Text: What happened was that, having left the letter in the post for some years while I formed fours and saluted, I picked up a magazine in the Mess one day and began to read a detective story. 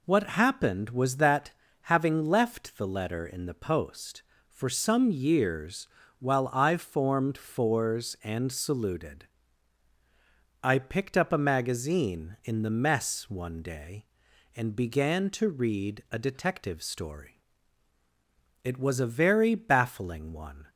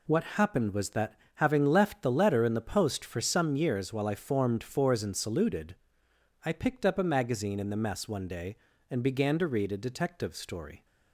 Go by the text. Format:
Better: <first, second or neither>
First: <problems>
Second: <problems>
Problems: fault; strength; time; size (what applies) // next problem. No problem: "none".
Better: second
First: pauses between "years" and "while"; slight; at 5.8 s; 0.32 s long // goes on to say "It was a very baffling one"; strong; from 18.6 s on; 2.0 s long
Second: none